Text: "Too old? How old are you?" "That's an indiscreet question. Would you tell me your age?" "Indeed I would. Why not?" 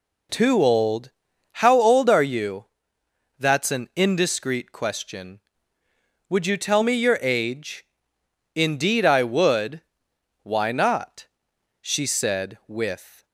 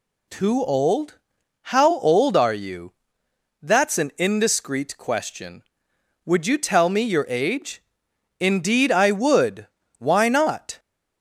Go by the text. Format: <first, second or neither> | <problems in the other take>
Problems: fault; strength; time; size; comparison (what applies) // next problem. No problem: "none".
second | goes on to say "she said with"; from 11.8 s on; 1.4 s long